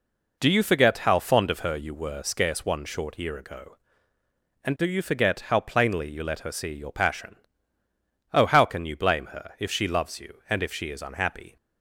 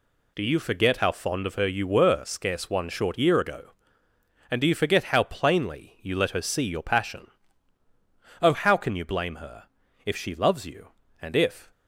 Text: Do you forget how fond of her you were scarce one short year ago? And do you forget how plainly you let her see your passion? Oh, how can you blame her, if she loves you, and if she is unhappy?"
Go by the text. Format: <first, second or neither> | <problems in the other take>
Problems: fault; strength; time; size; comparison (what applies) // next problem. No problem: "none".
first | stops before "she is unhappy"; at 11.7 s